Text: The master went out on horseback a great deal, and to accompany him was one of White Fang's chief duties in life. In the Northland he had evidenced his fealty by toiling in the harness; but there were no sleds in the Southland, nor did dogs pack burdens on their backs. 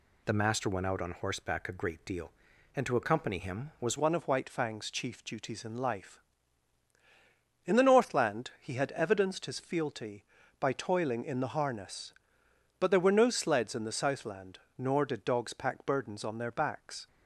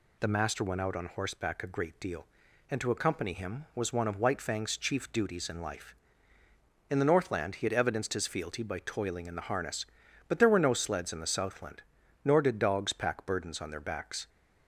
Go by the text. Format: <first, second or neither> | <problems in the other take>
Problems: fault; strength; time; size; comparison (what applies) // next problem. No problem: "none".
second | changes voice at "one"; from 3.9 s on; 13.1 s long